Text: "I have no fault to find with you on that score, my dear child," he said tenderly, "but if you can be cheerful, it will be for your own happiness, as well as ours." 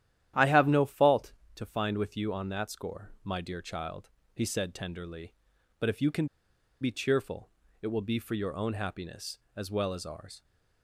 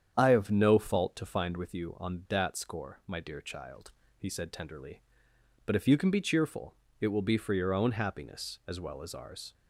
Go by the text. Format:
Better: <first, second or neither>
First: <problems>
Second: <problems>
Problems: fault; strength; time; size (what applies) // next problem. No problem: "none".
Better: second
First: starts louder than the rest; strong; until 1.5 s; 11.5 dB // pauses between "can" and "be"; noticeable; at 6.2 s; 0.54 s long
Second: starts louder than the rest; strong; until 1.1 s; 8.5 dB